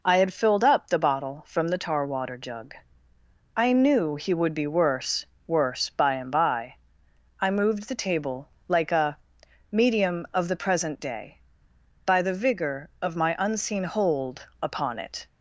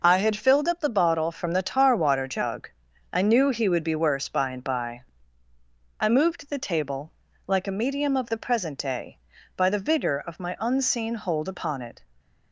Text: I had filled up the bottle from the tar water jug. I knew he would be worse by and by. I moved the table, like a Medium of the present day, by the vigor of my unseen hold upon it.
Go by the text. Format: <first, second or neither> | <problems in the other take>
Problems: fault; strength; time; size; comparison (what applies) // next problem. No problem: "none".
second | says "worse" twice; at 5.4 s // pauses between "a" and "Medium"; noticeable; at 9.1 s; 0.52 s long